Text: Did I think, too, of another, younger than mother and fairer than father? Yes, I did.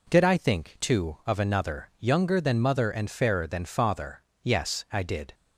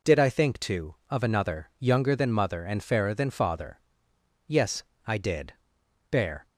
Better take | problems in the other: first | goes on to say "Bear"; slight; from 6.1 s on; 0.36 s long

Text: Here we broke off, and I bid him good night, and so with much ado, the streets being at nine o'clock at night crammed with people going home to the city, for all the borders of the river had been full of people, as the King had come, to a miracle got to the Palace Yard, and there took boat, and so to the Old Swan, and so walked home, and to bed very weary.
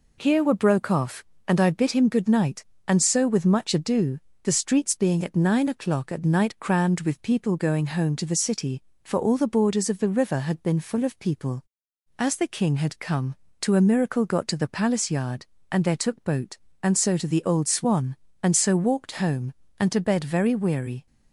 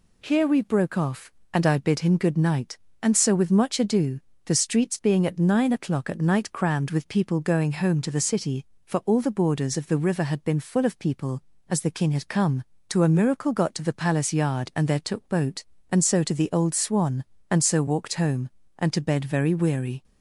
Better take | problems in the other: second | says "were" for "we"; at 0.4 s

